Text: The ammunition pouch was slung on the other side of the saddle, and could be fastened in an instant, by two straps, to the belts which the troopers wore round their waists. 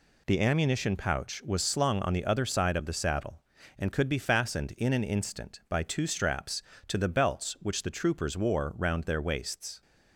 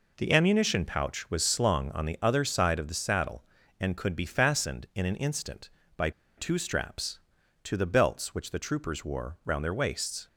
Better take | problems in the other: first | pauses between "by" and "two"; slight; at 6.1 s; 0.26 s long

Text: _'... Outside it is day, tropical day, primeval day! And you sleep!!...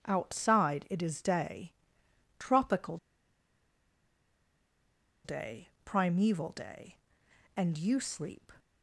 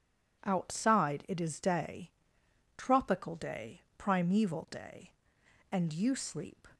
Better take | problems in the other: second | pauses between "tropical" and "day"; strong; at 2.9 s; 2.2 s long

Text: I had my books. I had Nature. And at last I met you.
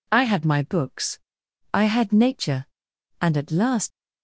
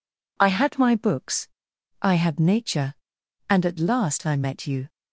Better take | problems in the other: second | stops before "I met you"; at 3.9 s

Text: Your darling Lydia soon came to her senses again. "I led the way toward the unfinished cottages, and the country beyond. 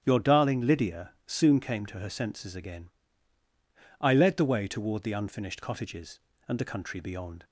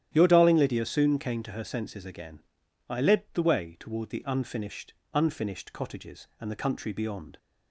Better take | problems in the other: first | starts louder than the rest; strong; until 1.1 s; 11 dB; strong in the first // says "unfinished" twice; at 5.1 s

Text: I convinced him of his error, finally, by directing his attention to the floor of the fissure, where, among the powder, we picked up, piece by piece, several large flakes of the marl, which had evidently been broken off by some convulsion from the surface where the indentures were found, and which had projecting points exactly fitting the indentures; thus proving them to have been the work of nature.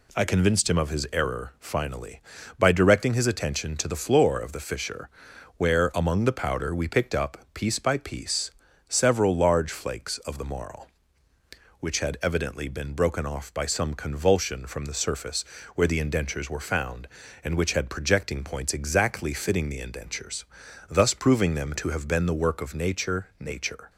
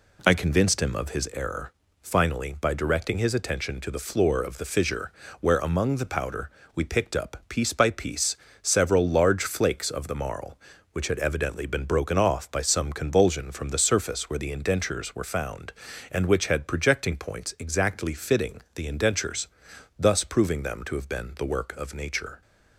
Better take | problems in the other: second | pauses between "surface" and "where"; slight; at 15.4 s; 0.32 s long // says "nature" twice; at 23.3 s

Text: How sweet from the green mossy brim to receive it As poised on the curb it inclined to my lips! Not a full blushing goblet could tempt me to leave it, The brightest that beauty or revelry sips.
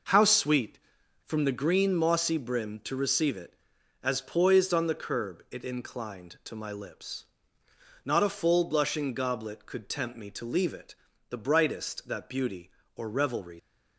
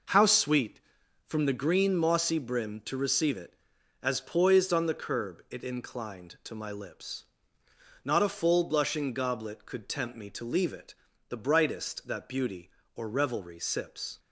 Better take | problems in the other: second | stops before "sips"; at 13.5 s

